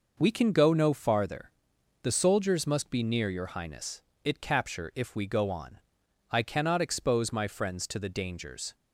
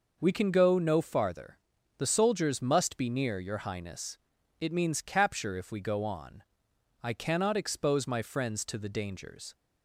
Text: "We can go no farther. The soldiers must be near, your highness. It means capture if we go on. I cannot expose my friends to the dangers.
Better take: second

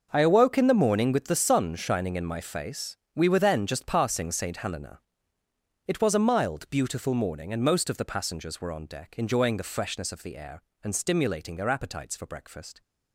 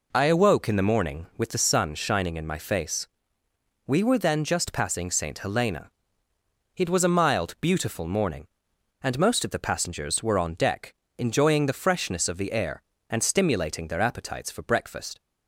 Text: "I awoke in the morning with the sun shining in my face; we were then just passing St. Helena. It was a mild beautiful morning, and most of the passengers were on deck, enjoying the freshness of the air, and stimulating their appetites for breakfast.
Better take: second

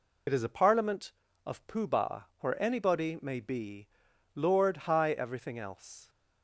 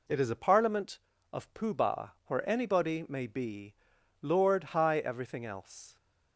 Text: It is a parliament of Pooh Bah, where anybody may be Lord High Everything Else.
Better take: second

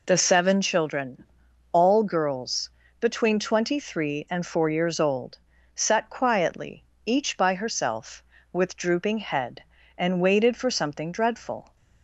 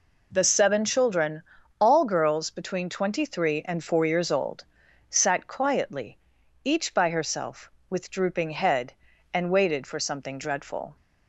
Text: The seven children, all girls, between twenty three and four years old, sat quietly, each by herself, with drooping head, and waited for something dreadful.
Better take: neither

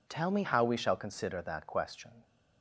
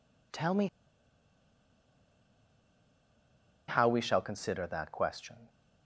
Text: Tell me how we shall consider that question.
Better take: first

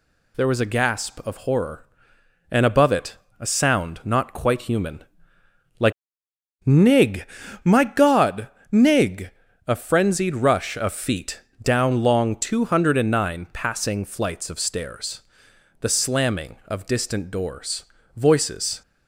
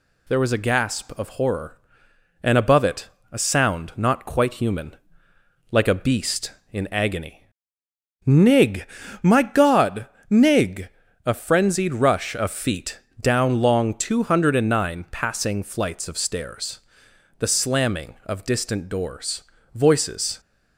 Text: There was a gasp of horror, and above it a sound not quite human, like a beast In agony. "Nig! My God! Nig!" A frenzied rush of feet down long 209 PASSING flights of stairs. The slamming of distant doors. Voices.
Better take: second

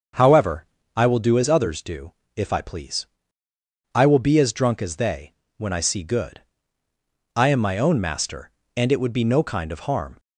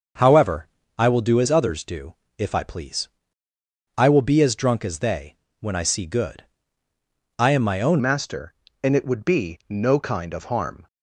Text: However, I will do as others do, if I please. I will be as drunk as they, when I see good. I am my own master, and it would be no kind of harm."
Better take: first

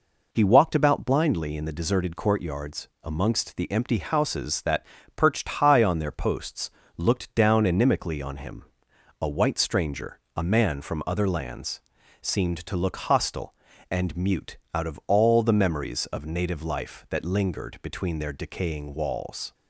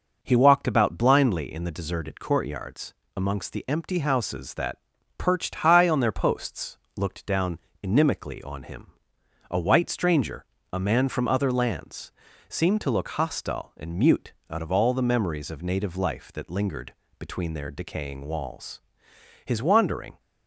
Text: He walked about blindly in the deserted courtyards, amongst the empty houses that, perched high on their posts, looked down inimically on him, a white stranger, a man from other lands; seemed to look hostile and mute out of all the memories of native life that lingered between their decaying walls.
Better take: first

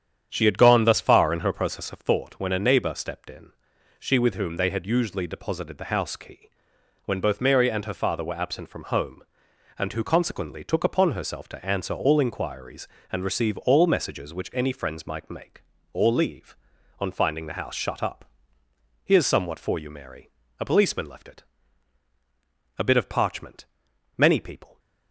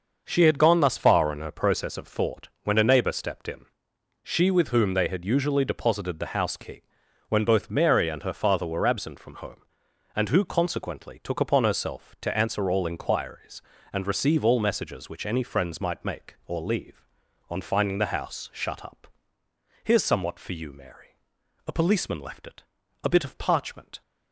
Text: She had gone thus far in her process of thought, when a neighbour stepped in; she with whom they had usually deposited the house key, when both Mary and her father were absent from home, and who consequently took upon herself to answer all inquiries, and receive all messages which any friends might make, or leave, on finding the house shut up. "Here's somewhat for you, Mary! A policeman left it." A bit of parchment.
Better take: second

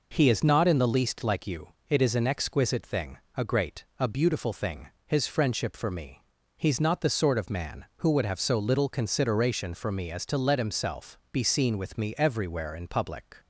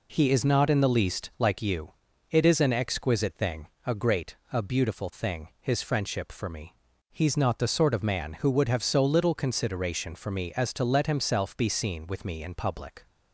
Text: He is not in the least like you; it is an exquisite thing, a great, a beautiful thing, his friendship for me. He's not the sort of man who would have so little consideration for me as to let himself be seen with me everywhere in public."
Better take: first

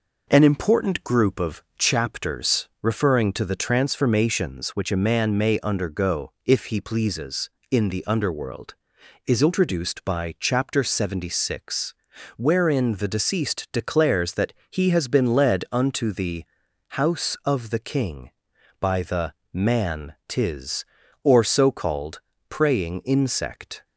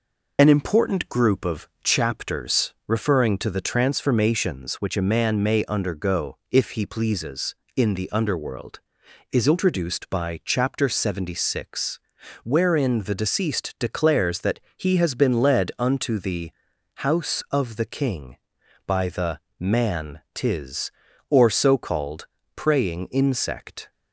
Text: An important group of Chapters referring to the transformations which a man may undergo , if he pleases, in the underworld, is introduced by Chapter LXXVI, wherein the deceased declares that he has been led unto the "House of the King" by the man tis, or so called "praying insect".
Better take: first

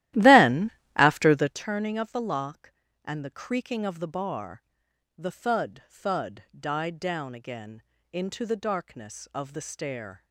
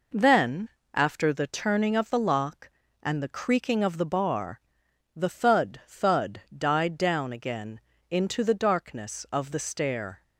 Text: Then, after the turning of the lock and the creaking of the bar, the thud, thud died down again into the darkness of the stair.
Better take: second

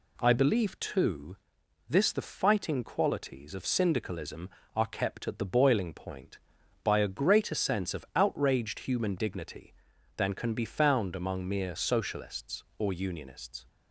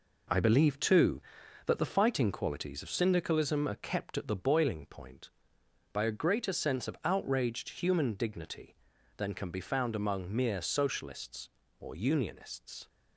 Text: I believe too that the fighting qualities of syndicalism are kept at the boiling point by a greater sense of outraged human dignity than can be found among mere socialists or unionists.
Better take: second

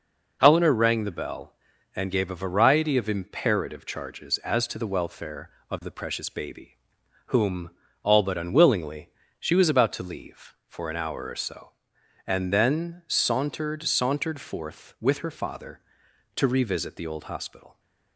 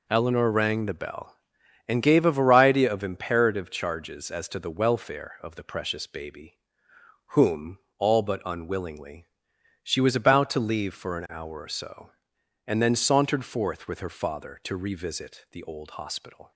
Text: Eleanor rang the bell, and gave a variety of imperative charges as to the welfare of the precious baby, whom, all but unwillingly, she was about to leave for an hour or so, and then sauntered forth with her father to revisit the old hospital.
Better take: second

